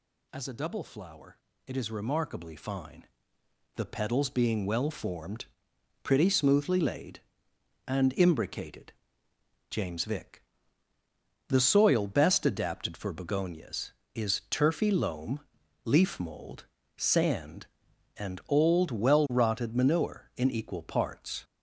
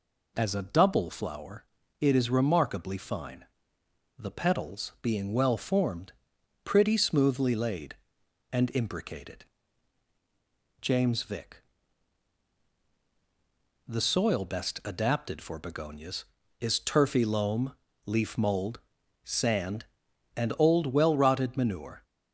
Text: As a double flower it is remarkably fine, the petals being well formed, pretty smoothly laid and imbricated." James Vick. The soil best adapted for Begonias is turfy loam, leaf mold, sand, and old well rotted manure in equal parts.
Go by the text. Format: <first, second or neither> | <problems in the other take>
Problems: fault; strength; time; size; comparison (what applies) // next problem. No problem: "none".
first | pauses between "flower" and "it"; at 1.6 s; 0.38 s long; slight in the first // stops before "in equal parts"; at 22.0 s